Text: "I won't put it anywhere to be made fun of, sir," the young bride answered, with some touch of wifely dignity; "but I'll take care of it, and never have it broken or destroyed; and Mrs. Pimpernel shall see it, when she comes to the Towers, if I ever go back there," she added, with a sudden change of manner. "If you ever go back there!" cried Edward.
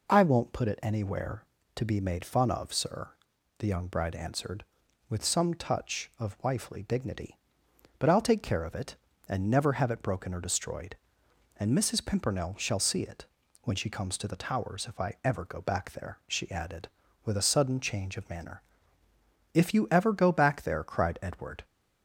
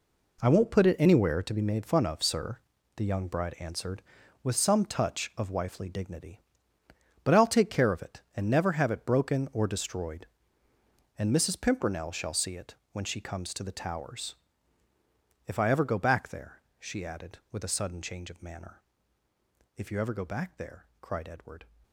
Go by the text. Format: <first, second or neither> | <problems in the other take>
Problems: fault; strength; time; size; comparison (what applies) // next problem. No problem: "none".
first | gets quieter; strong; throughout; 10.5 dB